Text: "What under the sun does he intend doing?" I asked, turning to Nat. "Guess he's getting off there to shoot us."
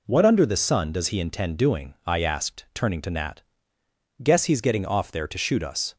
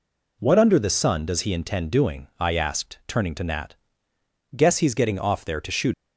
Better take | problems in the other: first | stops before "us"; at 5.9 s

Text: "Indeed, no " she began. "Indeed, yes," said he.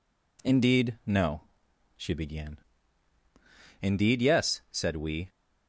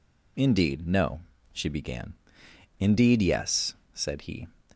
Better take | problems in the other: second | says "we" for "he"; at 4.9 s

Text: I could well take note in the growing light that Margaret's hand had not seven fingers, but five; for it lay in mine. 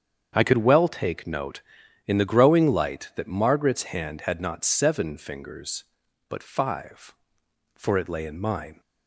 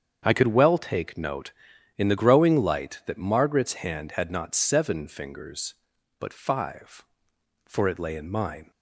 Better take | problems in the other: neither | starts louder than the rest; strong; the same in both

